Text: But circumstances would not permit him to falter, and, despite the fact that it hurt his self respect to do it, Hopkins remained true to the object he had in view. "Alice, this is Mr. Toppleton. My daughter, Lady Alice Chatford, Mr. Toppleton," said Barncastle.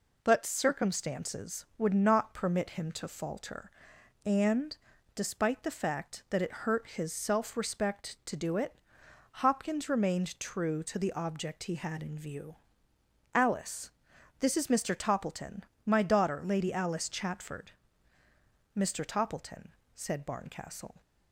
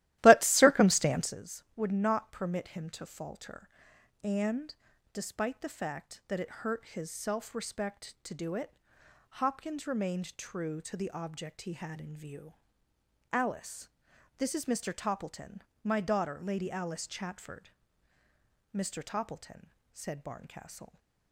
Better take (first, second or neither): first